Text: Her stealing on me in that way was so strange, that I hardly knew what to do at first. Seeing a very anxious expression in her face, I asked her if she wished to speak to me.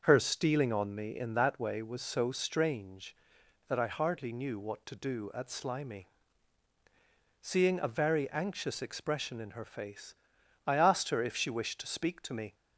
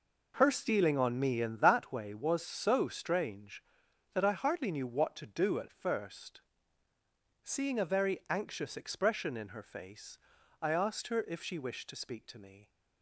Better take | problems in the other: second | starts louder than the rest; until 1.0 s; 6.5 dB // says "slimy" for "first"; at 5.4 s

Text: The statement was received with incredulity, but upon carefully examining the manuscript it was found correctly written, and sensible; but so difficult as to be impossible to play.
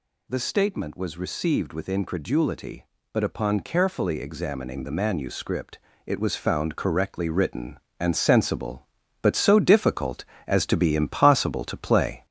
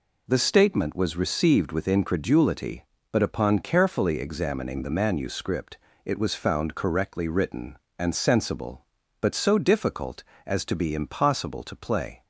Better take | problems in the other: second | gets louder; slight; throughout; 3 dB // pauses between "manuscript" and "it"; slight; at 5.7 s; 0.26 s long; slight in the second

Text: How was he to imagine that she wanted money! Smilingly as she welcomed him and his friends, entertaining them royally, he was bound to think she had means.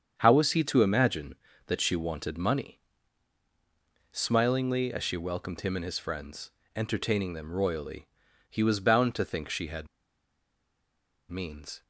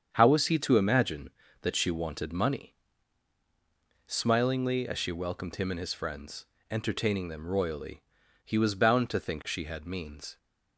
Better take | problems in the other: second | starts louder than the rest; strong; until 1.1 s; 7.5 dB; strong in the second // pauses between "had" and "means"; strong; at 9.8 s; 1.4 s long

